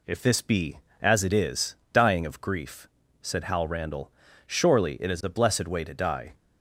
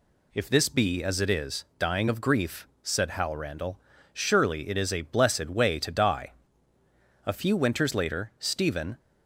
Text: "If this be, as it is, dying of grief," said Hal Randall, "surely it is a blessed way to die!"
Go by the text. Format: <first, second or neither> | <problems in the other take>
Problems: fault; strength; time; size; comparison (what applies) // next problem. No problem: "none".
first | goes on to say "A few winters later Stephen"; strong; from 7.2 s on; 1.7 s long